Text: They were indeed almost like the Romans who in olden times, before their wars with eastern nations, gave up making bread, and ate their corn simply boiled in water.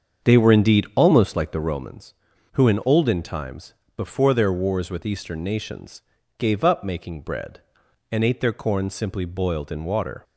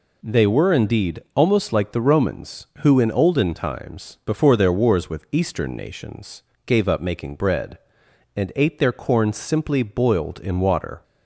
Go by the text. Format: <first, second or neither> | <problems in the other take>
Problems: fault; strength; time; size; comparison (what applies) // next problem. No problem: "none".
second | starts louder than the rest; strong; until 1.8 s; 7.5 dB